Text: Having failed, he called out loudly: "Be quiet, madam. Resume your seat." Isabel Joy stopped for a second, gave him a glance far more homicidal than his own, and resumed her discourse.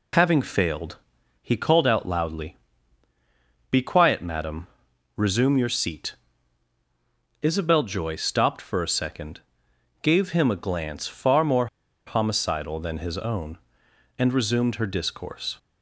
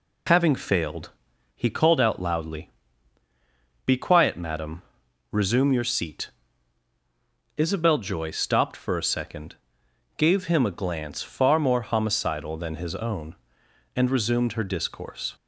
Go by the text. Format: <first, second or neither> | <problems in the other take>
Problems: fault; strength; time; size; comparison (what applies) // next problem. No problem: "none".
second | pauses between "more" and "homicidal"; at 11.6 s; 0.40 s long